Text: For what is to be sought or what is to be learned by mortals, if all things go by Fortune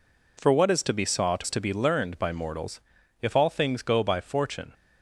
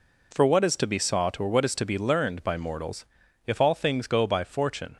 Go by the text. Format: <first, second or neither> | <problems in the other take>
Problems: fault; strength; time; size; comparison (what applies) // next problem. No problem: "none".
second | skips "or what"; at 1.4 s